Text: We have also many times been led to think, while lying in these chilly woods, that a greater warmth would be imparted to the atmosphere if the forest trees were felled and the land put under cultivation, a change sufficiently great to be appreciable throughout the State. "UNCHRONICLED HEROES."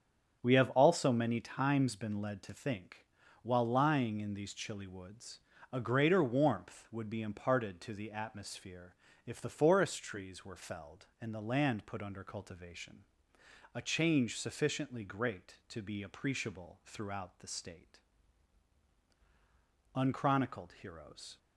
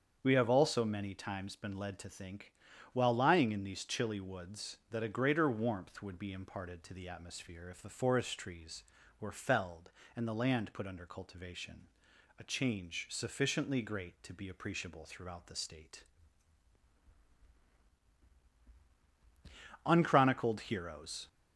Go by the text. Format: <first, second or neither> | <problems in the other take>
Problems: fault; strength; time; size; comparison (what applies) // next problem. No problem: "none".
second | starts louder than the rest; strong; until 1.4 s; 7.5 dB; strong in the second // skips "that"; at 5.5 s // pauses between "atmosphere" and "if"; slight; at 8.9 s; 0.32 s long